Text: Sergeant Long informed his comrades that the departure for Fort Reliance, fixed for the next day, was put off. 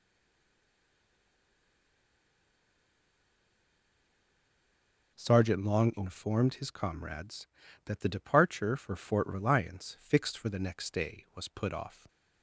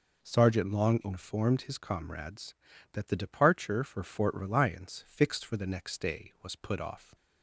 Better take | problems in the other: second | stays silent before the first word; strong; until 5.1 s; 5.1 s long

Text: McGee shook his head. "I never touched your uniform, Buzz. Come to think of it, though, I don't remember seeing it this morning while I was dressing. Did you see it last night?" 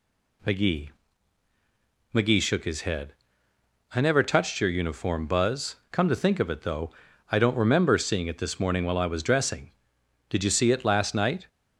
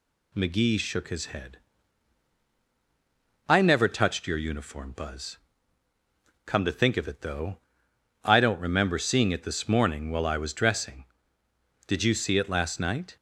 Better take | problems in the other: second | says "McGee" twice; at 2.1 s

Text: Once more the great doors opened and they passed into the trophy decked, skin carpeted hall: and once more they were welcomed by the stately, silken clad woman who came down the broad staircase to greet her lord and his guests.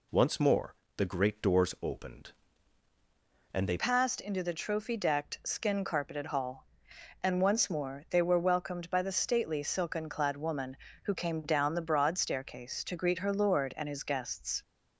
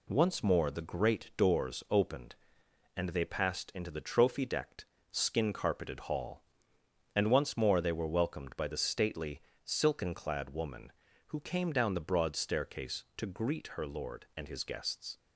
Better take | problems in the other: second | pauses between "more" and "the"; slight; at 0.7 s; 0.22 s long // changes voice at "passed"; from 3.7 s on; 10.9 s long

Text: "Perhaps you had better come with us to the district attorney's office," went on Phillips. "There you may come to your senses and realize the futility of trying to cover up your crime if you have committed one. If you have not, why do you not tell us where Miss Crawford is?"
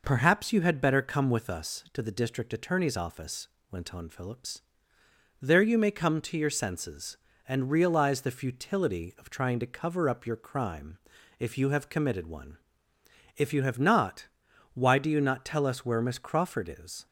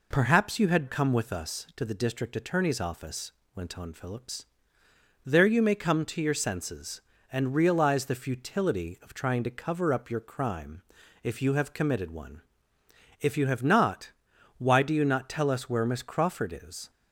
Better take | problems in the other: first | skips "better"; at 0.8 s // pauses between "crime" and "if"; at 10.8 s; 0.42 s long; also in the first

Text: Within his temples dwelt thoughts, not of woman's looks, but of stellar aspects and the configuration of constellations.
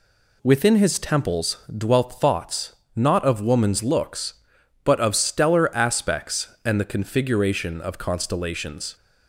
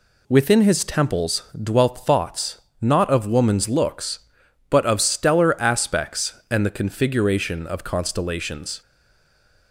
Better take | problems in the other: first | pauses between "temples" and "dwelt"; slight; at 1.4 s; 0.20 s long; slight in the first // stays silent after the last word; slight; from 8.8 s on; 0.9 s long

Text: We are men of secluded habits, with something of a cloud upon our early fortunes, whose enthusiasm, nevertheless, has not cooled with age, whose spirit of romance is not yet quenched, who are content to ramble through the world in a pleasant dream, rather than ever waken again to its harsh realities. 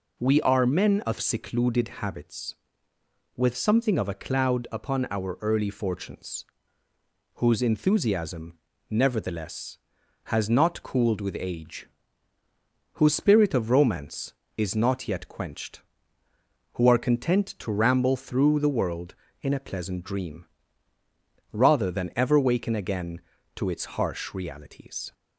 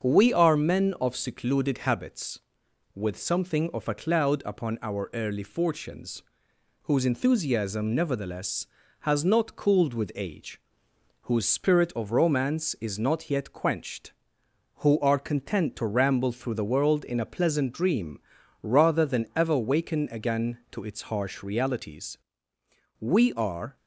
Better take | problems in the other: first | starts louder than the rest; strong; until 1.0 s; 7 dB // goes on to say "We are"; noticeable; from 22.9 s on; 0.76 s long

